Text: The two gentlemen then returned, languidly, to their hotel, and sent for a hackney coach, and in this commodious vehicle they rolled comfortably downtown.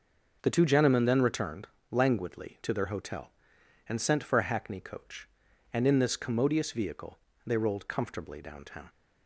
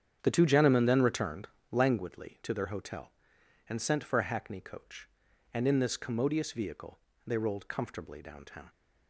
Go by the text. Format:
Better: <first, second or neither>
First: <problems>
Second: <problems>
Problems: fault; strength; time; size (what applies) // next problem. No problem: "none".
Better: first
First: pauses between "vehicle" and "they"; slight; at 7.1 s; 0.28 s long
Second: starts louder than the rest; strong; until 2.0 s; 8.5 dB // pauses between "vehicle" and "they"; slight; at 6.9 s; 0.28 s long